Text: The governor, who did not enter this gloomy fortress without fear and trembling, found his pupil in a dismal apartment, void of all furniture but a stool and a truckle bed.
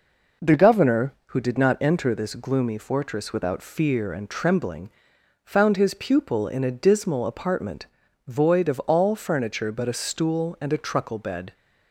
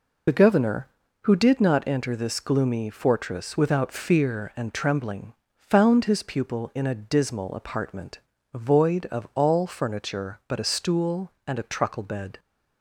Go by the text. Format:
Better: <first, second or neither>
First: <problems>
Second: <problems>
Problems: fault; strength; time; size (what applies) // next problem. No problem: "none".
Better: first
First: none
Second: loses the start of "The"; at 0.2 s; 45 ms